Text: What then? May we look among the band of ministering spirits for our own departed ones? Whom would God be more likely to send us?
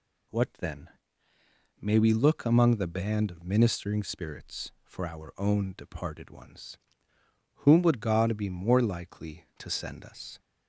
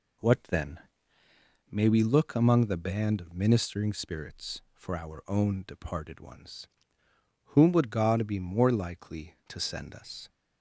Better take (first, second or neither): first